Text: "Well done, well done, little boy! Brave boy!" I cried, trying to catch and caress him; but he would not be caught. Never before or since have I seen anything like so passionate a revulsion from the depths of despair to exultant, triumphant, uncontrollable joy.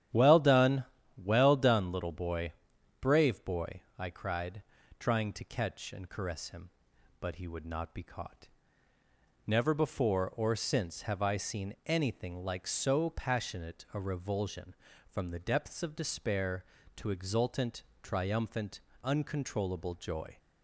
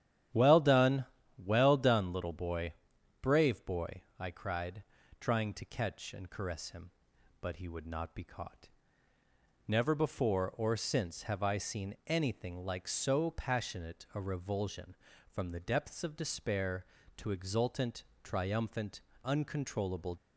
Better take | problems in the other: first | starts louder than the rest; strong; until 1.6 s; 10.5 dB; strong in the first // stops before "joy"; at 20.1 s

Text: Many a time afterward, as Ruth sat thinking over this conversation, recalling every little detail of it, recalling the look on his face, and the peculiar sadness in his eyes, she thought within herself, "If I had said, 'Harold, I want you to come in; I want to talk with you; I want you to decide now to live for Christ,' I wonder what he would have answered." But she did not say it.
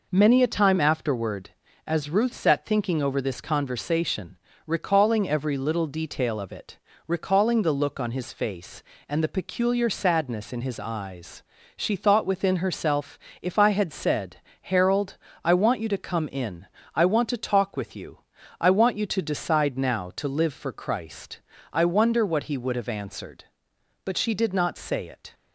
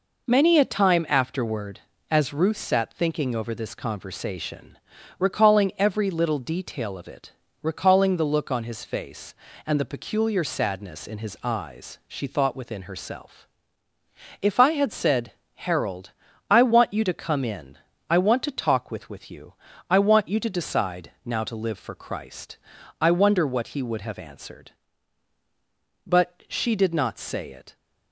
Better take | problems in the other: first | says "with" twice; at 19.0 s

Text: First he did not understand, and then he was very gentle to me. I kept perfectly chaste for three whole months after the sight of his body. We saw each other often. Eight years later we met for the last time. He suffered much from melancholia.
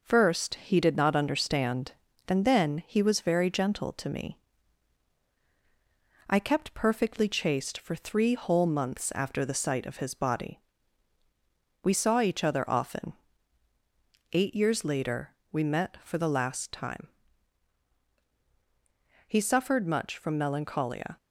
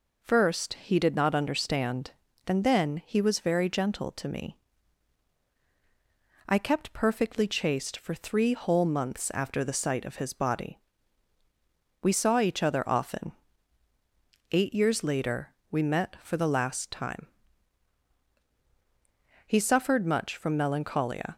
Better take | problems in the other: second | gets quieter; slight; throughout; 3 dB // pauses between "later" and "we"; slight; at 15.3 s; 0.16 s long; slight in the second

